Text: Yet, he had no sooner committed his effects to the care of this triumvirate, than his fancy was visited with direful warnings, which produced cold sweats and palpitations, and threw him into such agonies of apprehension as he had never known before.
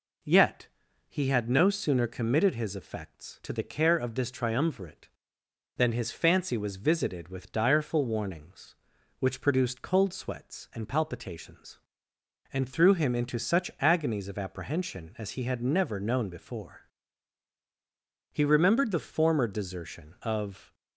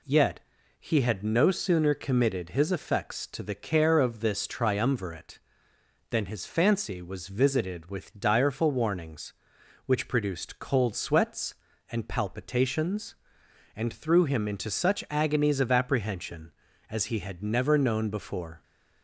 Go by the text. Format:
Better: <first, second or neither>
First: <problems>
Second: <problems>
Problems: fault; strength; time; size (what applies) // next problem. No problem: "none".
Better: second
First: goes on to say "He remembered the former desertion of"; strong; from 18.3 s on; 2.4 s long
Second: none